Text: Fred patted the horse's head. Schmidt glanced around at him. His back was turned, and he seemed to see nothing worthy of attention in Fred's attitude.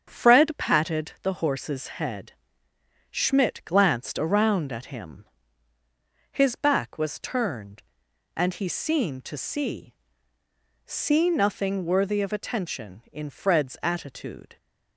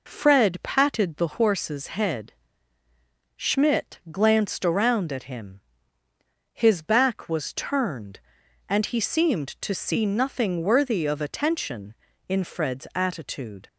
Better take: second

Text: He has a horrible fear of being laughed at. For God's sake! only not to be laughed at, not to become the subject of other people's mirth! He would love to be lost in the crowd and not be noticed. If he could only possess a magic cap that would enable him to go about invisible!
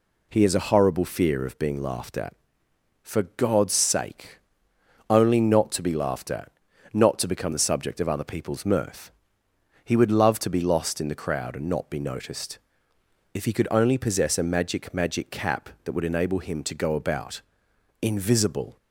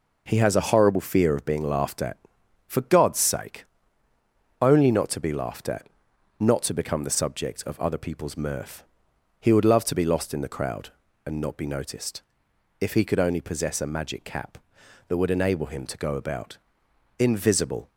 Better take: second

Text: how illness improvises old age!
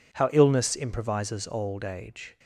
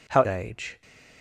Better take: first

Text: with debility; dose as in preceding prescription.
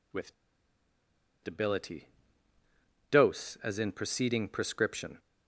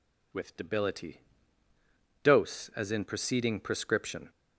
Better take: second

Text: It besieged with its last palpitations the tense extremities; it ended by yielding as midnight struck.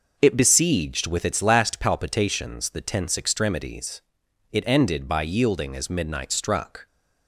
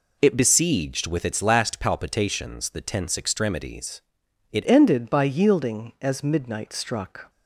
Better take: first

